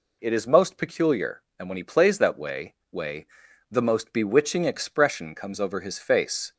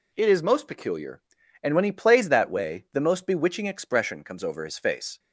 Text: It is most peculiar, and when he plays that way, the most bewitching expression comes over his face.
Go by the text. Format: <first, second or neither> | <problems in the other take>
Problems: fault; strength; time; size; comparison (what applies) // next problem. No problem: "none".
second | says "way" twice; at 2.9 s